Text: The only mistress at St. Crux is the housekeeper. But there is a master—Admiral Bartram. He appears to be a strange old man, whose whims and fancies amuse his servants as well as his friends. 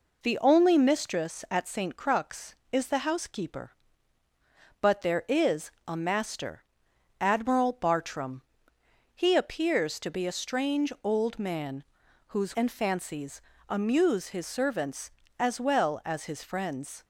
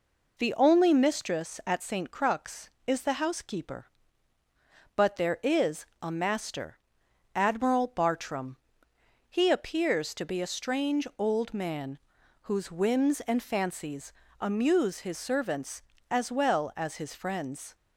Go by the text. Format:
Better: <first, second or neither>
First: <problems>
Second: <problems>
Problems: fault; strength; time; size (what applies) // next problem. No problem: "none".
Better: second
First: pauses between "is" and "a"; slight; at 5.7 s; 0.16 s long // skips "whims"; at 12.5 s // pauses between "fancies" and "amuse"; slight; at 13.4 s; 0.26 s long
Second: pauses between "is" and "a"; slight; at 5.8 s; 0.16 s long // pauses between "fancies" and "amuse"; slight; at 14.1 s; 0.26 s long